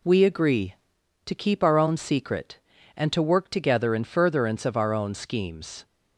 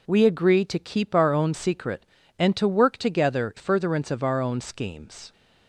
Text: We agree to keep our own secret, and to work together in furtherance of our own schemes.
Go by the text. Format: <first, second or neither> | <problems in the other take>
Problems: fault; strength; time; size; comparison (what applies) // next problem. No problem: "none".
first | skips "in"; at 3.5 s